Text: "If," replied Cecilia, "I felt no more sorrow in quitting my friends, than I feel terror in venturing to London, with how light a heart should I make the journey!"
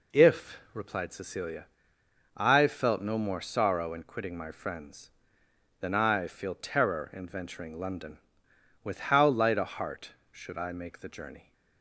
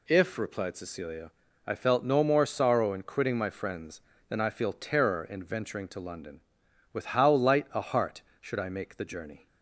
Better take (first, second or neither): second